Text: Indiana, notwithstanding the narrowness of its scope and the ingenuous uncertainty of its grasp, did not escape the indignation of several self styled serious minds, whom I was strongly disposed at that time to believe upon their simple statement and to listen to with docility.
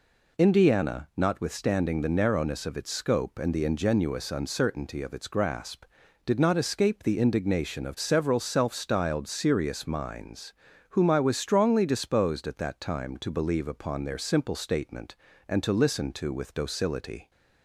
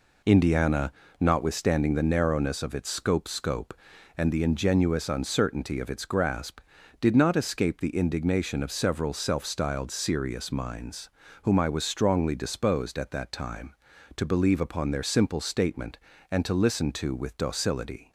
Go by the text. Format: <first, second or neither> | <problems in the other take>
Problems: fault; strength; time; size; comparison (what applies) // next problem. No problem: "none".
first | says "scope" twice; at 3.2 s